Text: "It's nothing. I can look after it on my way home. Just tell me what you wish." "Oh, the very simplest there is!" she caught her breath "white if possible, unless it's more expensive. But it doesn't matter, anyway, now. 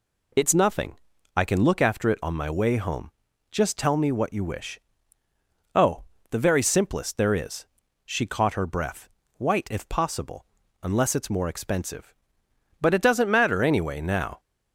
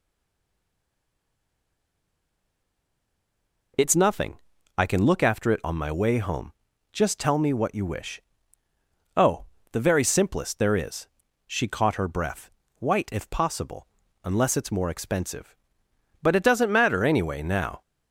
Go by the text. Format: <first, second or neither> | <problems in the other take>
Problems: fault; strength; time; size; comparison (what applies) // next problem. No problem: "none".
first | stays silent before the first word; strong; until 3.7 s; 3.7 s long // pauses between "breath" and "white"; slight; at 12.5 s; 0.28 s long; slight in the first